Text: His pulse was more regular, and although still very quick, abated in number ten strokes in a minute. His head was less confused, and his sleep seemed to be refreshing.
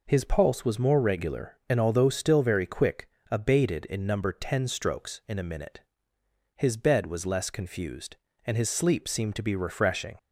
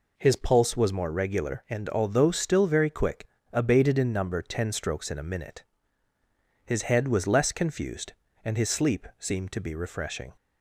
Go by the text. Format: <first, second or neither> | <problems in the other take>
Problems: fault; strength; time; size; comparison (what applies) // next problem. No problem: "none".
second | says "bed" for "head"; at 6.7 s